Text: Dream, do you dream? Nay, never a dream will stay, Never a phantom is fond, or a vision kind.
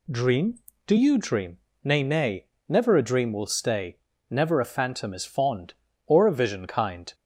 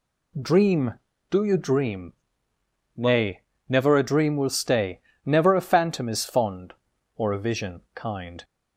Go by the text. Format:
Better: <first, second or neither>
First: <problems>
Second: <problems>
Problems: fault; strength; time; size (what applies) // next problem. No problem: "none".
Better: second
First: says "Nay" twice; at 2.0 s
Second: none